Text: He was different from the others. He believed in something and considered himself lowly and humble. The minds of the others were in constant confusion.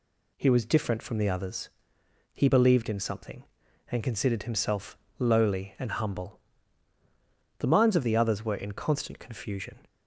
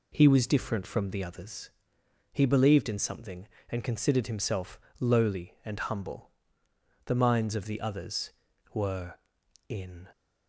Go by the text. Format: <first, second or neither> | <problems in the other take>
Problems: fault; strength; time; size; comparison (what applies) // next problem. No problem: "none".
first | pauses between "himself" and "lowly"; slight; at 4.7 s; 0.22 s long; slight in the first // stops before "constant confusion"; at 10.1 s